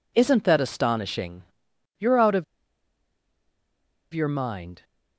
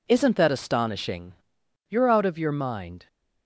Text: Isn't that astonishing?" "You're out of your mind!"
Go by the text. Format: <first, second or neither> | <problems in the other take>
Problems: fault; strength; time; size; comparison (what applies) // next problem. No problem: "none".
second | pauses between "of" and "your"; strong; at 2.4 s; 1.6 s long